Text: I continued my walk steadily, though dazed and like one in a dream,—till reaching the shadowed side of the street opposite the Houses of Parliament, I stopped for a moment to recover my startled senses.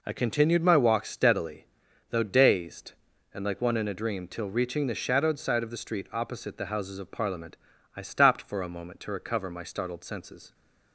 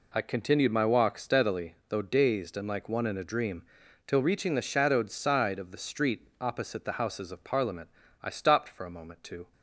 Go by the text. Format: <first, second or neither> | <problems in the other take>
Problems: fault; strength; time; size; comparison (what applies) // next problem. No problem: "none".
first | stops before "recover my startled senses"; at 9.5 s